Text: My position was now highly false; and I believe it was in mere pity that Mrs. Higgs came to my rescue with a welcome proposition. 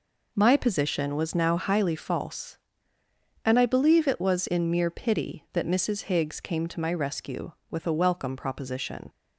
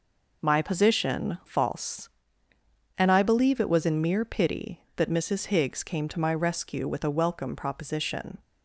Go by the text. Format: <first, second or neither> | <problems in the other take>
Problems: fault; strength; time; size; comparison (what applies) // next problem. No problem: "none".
first | skips "was now highly"; at 1.4 s